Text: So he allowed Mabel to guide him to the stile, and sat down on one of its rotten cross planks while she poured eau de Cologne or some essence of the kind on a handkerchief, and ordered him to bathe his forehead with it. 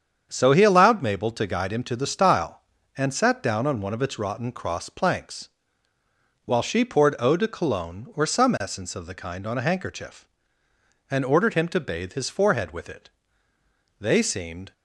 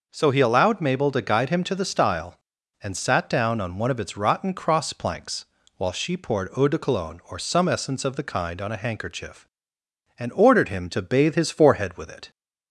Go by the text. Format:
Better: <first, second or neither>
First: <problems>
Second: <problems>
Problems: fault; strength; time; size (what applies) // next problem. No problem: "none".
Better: second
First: starts louder than the rest; strong; until 1.3 s; 7.5 dB // pauses between "planks" and "while"; noticeable; at 5.4 s; 0.98 s long // goes on to say "They seemed"; noticeable; from 13.9 s on; 0.74 s long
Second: pauses between "planks" and "while"; slight; at 5.4 s; 0.32 s long